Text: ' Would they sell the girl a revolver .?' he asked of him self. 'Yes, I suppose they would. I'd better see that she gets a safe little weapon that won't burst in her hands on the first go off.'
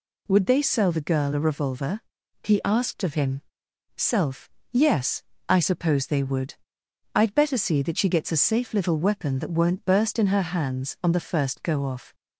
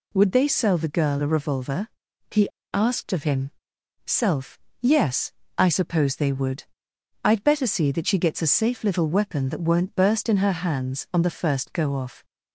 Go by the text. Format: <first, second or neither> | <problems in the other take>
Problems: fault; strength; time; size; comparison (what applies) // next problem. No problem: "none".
first | pauses between "he" and "asked"; slight; at 2.4 s; 0.27 s long // pauses between "him" and "self"; noticeable; at 3.5 s; 0.54 s long; noticeable in the first